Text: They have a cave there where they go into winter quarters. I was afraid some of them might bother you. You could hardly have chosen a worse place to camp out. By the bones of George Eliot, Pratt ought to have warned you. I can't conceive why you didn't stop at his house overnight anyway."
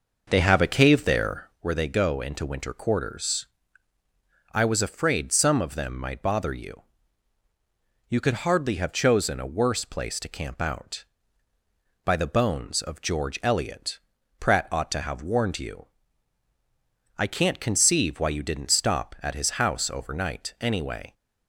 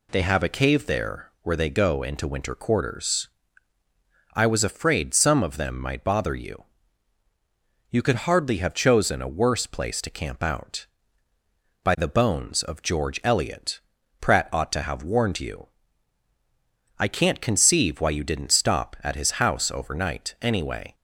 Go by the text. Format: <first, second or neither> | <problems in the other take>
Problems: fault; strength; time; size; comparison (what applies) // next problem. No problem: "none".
second | starts louder than the rest; noticeable; until 1.7 s; 5.5 dB